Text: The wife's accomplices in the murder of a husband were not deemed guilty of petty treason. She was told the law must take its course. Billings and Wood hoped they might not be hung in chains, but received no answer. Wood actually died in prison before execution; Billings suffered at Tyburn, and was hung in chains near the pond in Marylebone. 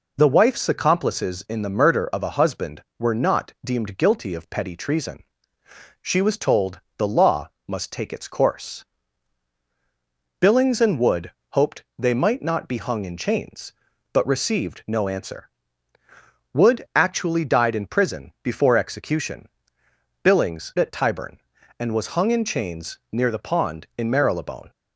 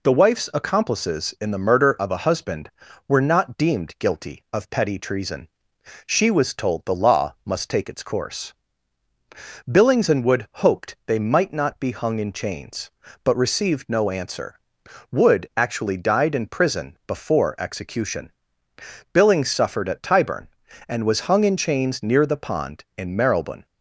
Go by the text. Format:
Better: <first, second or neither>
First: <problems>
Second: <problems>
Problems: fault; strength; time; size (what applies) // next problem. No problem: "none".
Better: second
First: pauses between "told" and "the"; slight; at 6.7 s; 0.18 s long // pauses between "law" and "must"; slight; at 7.4 s; 0.18 s long // pauses between "Wood" and "hoped"; slight; at 11.3 s; 0.16 s long // pauses between "hoped" and "they"; slight; at 11.8 s; 0.16 s long // skips "suffered"; at 20.7 s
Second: none